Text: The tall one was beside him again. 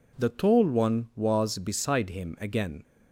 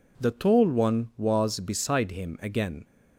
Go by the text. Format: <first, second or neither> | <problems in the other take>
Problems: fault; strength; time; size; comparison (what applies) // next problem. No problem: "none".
neither | none